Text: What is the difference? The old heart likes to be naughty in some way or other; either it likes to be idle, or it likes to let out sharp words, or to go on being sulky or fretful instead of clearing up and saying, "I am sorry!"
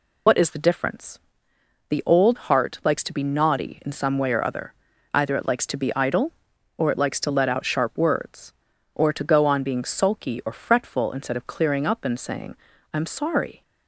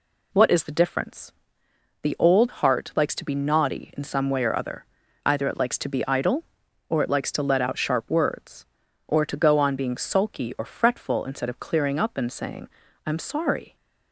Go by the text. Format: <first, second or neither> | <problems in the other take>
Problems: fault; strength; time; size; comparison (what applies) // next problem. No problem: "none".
second | loses the start of "What"; at 0.2 s; 80 ms